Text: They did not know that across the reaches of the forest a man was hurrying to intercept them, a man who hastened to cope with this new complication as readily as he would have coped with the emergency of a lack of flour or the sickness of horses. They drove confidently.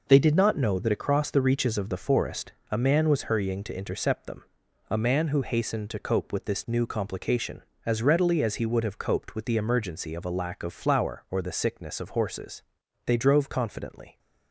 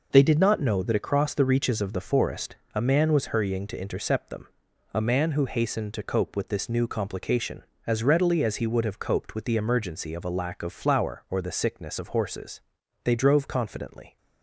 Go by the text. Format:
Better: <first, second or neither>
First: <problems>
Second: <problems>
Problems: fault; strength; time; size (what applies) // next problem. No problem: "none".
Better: neither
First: pauses between "forest" and "a"; slight; at 2.5 s; 0.20 s long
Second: pauses between "forest" and "a"; slight; at 2.5 s; 0.20 s long